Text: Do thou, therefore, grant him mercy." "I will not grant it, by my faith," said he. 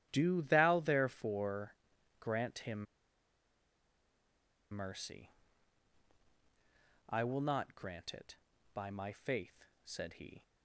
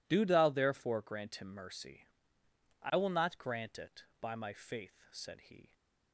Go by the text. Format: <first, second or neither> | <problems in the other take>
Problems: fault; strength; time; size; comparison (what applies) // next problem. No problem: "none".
second | starts louder than the rest; strong; until 1.1 s; 11.5 dB // pauses between "him" and "mercy"; strong; at 2.8 s; 1.8 s long